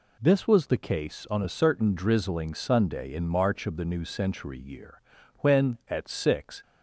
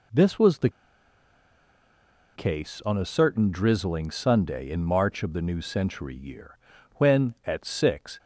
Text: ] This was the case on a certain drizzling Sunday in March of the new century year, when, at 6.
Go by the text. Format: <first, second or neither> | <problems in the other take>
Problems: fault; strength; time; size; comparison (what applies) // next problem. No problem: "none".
first | pauses between "the" and "case"; strong; at 0.6 s; 1.6 s long